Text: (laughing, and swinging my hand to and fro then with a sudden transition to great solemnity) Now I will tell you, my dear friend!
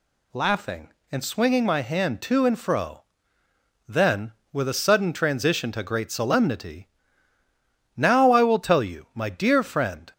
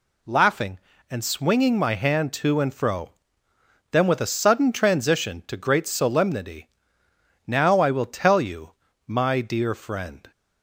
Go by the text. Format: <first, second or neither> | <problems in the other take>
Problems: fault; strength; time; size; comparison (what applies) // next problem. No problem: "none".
neither | pauses between "fro" and "then"; noticeable; the same in both